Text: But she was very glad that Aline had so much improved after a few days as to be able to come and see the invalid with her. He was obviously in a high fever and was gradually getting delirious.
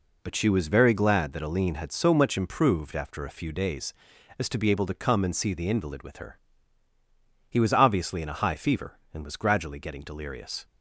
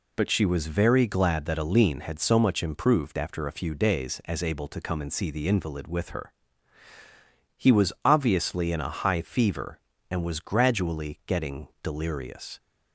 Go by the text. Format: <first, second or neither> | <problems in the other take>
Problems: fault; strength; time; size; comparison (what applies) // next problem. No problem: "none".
first | skips "to be"; at 4.4 s